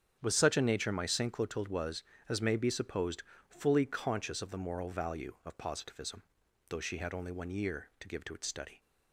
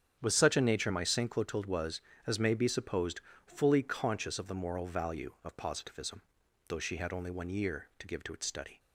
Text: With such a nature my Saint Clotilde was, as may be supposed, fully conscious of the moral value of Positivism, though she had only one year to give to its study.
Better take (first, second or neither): neither